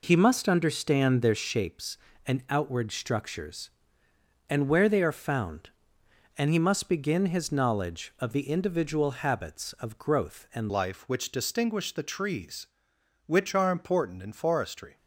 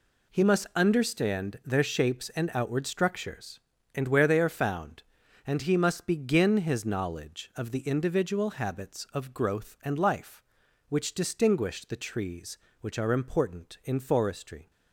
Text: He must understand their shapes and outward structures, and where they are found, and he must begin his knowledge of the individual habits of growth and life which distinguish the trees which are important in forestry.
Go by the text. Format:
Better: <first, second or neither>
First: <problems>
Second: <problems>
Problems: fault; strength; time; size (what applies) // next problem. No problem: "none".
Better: second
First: changes voice at "life"; from 10.6 s on; 4.3 s long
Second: none